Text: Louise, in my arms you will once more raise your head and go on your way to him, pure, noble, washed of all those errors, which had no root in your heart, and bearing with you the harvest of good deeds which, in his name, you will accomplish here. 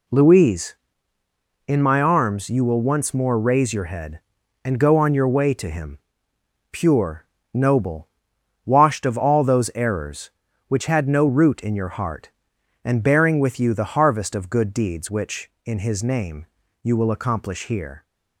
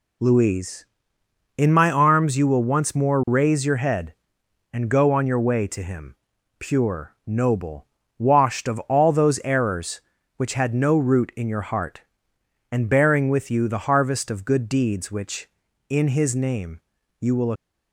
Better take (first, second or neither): first